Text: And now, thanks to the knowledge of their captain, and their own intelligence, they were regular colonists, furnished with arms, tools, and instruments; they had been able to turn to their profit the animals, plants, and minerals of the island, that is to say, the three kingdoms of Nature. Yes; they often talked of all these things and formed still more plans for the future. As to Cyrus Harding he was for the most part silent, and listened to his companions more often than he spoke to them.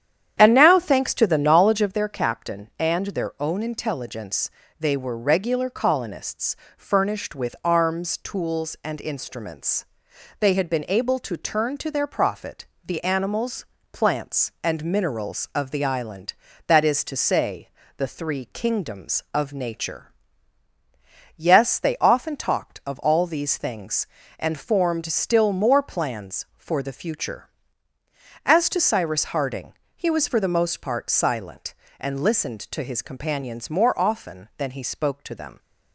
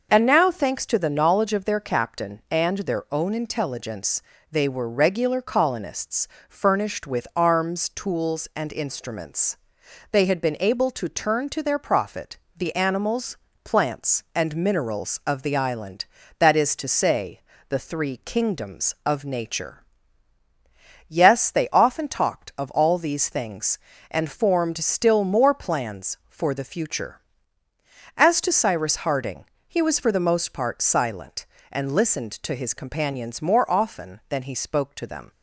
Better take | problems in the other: second | starts louder than the rest; strong; until 1.9 s; 9.5 dB // pauses between "profit" and "the"; slight; at 12.6 s; 0.18 s long; slight in the second // pauses between "Harding" and "he"; slight; at 29.7 s; 0.28 s long; slight in the second

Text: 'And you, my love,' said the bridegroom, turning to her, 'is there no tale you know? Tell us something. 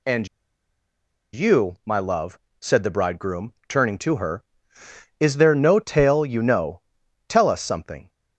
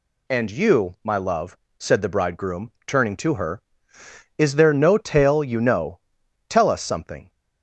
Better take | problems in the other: second | pauses between "And" and "you"; at 0.2 s; 1.0 s long

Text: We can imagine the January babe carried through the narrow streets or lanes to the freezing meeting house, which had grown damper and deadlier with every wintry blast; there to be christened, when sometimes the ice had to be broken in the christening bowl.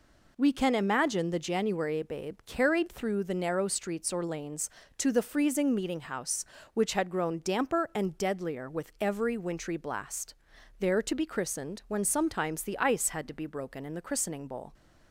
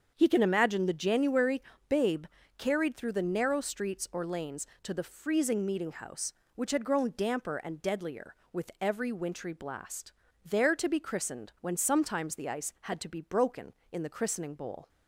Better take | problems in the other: first | starts louder than the rest; strong; until 1.1 s; 7 dB // says "He" for "We"; at 0.1 s // pauses between "January" and "babe"; slight; at 1.6 s; 0.28 s long // pauses between "babe" and "carried"; slight; at 2.2 s; 0.30 s long

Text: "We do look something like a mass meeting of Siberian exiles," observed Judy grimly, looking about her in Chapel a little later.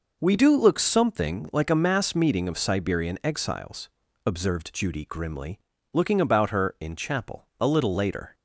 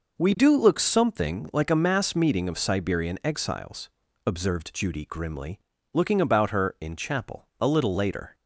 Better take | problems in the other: neither | none

